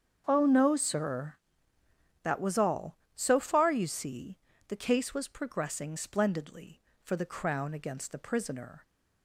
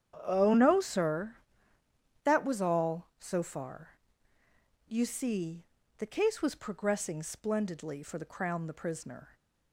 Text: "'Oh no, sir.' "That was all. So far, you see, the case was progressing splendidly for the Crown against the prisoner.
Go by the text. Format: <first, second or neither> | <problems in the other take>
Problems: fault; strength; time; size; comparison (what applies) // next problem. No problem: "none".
first | starts louder than the rest; strong; until 1.2 s; 9 dB; strong in the first // skips "against"; at 8.6 s